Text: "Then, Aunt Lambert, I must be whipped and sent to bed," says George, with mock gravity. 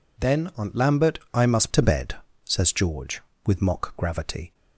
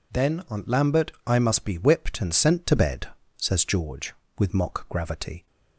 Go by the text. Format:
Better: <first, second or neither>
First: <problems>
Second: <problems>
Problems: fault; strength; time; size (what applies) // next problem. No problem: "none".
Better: second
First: skips "be whipped and sent"; at 1.7 s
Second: none